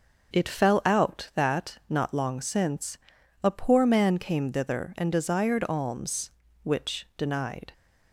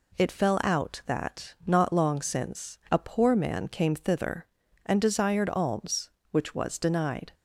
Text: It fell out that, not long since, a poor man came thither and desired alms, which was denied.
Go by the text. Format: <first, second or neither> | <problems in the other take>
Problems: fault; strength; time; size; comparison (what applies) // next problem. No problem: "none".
second | starts louder than the rest; until 1.4 s; 6.5 dB // skips "was"; at 7.1 s